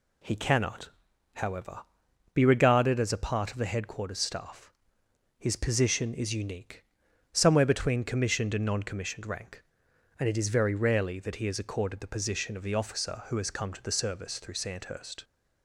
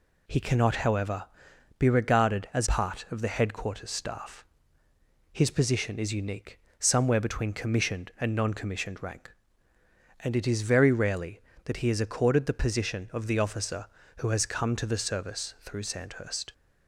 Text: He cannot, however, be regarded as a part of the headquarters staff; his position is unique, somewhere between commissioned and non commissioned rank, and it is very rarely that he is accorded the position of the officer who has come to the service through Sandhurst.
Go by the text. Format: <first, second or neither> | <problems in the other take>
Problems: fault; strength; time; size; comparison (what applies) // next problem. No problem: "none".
first | skips "a"; at 2.6 s